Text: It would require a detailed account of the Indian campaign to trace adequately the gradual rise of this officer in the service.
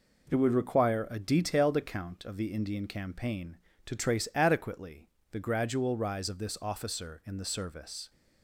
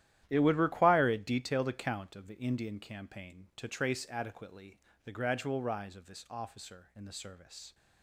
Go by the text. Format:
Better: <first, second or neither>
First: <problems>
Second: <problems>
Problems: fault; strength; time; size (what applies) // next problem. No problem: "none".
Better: first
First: pauses between "adequately" and "the"; slight; at 5.0 s; 0.22 s long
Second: gets quieter; strong; throughout; 13.5 dB // pauses between "adequately" and "the"; slight; at 4.7 s; 0.26 s long